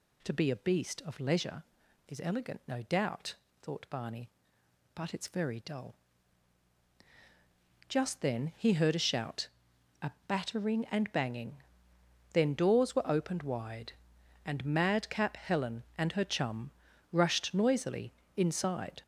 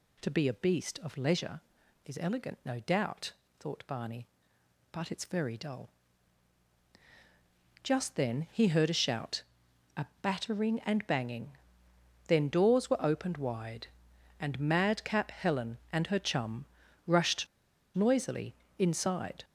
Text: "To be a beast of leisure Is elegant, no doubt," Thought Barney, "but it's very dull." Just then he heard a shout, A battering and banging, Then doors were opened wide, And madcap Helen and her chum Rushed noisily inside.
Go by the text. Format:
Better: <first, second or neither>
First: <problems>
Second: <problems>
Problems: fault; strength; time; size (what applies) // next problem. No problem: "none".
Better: first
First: pauses between "A" and "battering"; slight; at 10.1 s; 0.16 s long // pauses between "chum" and "Rushed"; at 16.6 s; 0.42 s long // pauses between "noisily" and "inside"; slight; at 18.1 s; 0.20 s long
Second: pauses between "A" and "battering"; slight; at 10.0 s; 0.16 s long // pauses between "chum" and "Rushed"; at 16.6 s; 0.42 s long // pauses between "Rushed" and "noisily"; noticeable; at 17.4 s; 0.47 s long // pauses between "noisily" and "inside"; slight; at 18.5 s; 0.20 s long